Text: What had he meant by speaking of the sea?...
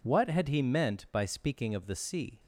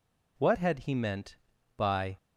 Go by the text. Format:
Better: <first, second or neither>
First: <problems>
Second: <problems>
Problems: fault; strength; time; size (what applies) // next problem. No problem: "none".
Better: first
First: none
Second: stops before "speaking of the sea"; at 2.1 s